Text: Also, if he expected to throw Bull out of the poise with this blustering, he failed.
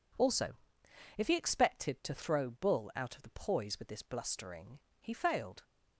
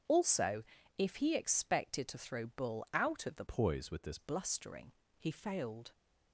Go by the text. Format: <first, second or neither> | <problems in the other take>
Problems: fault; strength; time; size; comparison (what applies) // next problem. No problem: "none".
first | starts louder than the rest; strong; until 1.4 s; 7.5 dB // changes voice from "poise" to "this"; from 3.4 to 4.1 s; 0.7 s long